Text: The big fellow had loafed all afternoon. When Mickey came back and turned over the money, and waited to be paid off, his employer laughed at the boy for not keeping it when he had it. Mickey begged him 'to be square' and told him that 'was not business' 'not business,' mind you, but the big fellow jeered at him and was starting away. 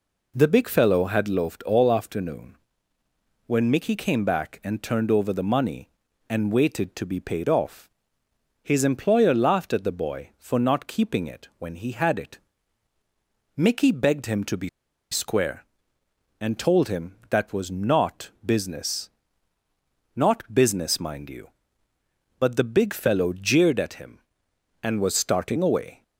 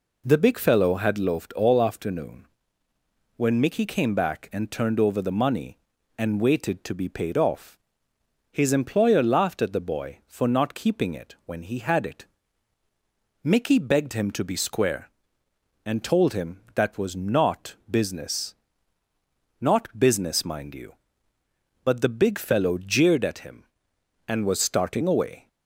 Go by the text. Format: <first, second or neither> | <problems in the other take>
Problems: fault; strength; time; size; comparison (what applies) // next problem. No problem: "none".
second | pauses between "be" and "square"; at 14.6 s; 0.42 s long // pauses between "not" and "business"; slight; at 18.2 s; 0.16 s long; slight in the second // pauses between "business" and "not"; at 19.0 s; 1.0 s long; also in the second